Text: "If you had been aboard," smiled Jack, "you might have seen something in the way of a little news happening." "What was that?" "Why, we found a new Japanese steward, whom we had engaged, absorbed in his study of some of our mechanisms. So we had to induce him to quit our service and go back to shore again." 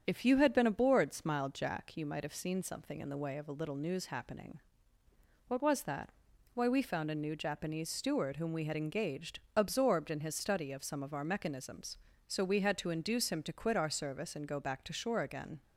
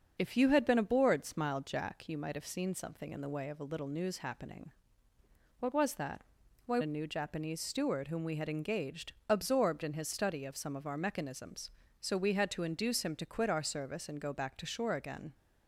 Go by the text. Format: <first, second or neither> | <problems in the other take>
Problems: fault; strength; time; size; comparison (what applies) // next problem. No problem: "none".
first | starts louder than the rest; until 1.1 s; 6.5 dB; strong in the first // skips "we found"; at 6.7 s